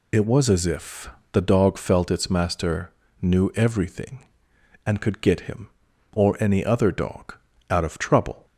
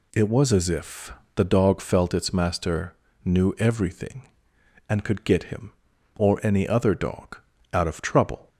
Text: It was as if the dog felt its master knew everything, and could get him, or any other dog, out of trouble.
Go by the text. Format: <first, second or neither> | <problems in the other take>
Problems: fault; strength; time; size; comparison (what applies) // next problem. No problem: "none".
second | loses the start of "It"; at 0.1 s; 35 ms // pauses between "if" and "the"; slight; at 1.0 s; 0.24 s long; slight in the second // pauses between "master" and "knew"; slight; at 2.9 s; 0.28 s long; slight in the second